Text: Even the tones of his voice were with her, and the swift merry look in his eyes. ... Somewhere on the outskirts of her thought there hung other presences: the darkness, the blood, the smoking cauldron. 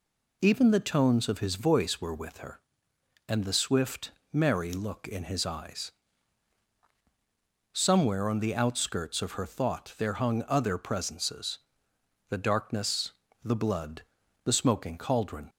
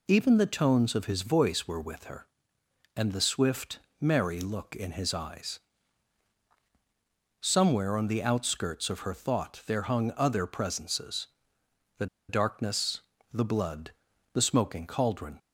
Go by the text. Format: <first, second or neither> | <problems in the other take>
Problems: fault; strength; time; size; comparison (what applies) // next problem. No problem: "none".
first | pauses between "swift" and "merry"; slight; at 3.7 s; 0.20 s long; slight in the first // pauses between "the" and "darkness"; slight; at 12.0 s; 0.23 s long